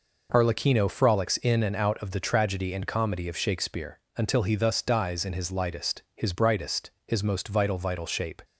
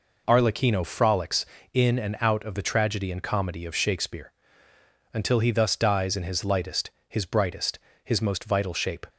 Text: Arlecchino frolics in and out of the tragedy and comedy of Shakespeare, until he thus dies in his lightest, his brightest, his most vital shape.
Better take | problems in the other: second | says "vital" twice; at 7.7 s

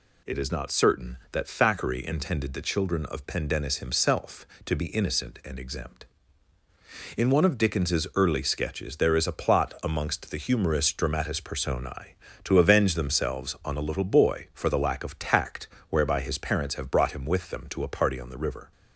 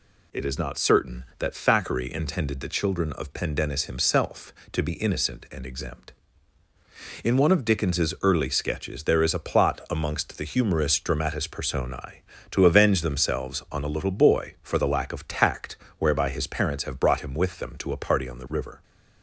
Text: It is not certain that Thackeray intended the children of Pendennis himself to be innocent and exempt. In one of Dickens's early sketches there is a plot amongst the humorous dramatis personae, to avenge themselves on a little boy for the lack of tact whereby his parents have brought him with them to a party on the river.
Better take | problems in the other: neither | pauses between "tact" and "whereby"; slight; the same in both

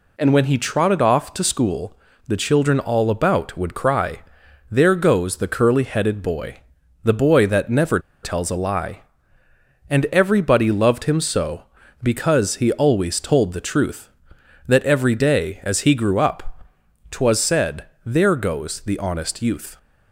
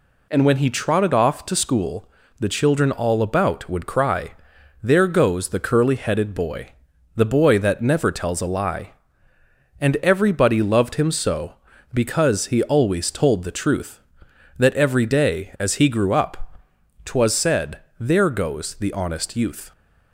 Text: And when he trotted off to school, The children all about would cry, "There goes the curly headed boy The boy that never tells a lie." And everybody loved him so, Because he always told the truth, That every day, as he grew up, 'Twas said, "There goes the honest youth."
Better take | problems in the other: second | pauses between "boy" and "The"; at 6.6 s; 0.44 s long; also in the second // pauses between "never" and "tells"; slight; at 8.0 s; 0.22 s long

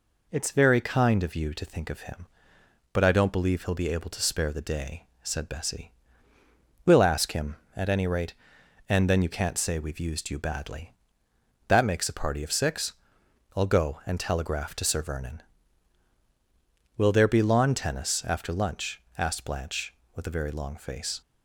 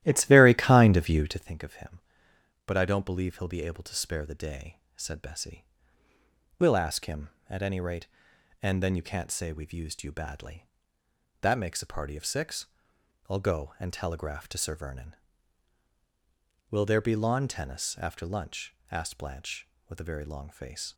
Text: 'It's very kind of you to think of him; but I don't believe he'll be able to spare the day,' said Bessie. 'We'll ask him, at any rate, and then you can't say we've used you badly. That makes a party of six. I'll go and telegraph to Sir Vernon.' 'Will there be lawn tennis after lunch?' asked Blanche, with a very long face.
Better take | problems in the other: first | starts louder than the rest; strong; until 1.5 s; 14 dB

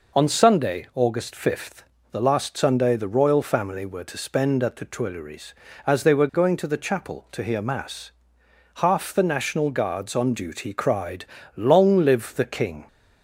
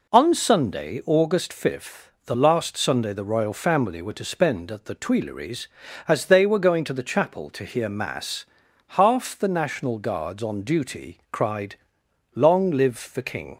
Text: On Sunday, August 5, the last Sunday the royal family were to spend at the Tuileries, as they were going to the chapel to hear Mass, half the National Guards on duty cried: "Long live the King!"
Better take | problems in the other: neither | none

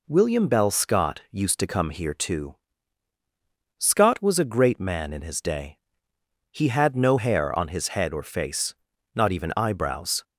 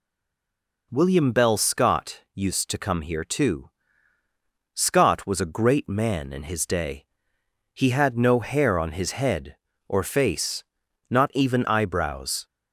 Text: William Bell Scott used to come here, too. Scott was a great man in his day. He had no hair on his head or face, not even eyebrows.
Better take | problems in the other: first | stays silent before the first word; slight; until 0.9 s; 0.9 s long

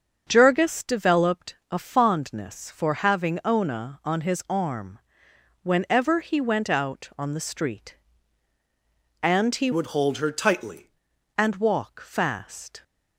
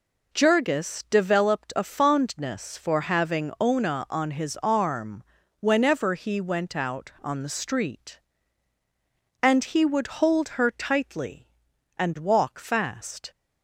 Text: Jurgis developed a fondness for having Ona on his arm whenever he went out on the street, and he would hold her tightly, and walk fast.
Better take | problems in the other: second | starts louder than the rest; until 1.2 s; 6.5 dB // pauses between "arm" and "whenever"; noticeable; at 4.9 s; 0.66 s long; slight in the second // changes voice from "would" to "tightly"; from 9.7 to 10.8 s; 1.1 s long

